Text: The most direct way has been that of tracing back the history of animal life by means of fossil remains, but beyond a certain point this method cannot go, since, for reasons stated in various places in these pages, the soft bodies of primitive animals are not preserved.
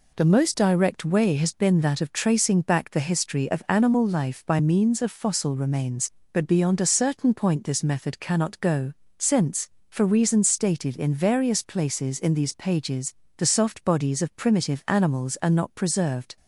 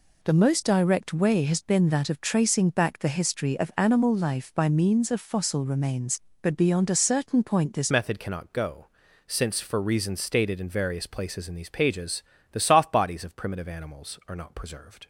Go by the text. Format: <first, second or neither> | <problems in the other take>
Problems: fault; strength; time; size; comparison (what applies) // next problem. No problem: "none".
first | changes voice at "method"; from 7.8 s on; 7.2 s long